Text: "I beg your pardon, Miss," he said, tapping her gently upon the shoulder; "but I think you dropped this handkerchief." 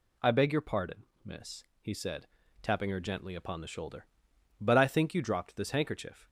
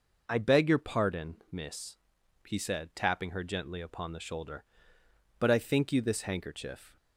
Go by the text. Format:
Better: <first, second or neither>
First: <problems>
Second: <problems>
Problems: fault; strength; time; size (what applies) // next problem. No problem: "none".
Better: first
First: none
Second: skips "dropped"; at 6.0 s